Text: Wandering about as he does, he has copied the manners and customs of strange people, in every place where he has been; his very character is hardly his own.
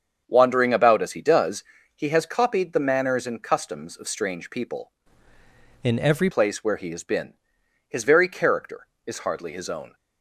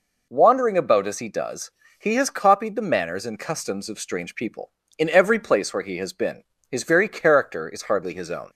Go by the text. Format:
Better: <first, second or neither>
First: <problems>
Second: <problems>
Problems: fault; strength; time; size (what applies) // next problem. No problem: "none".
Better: second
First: starts louder than the rest; strong; until 1.2 s; 7 dB // changes voice from "in" to "every"; from 5.8 to 6.2 s; 0.4 s long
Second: none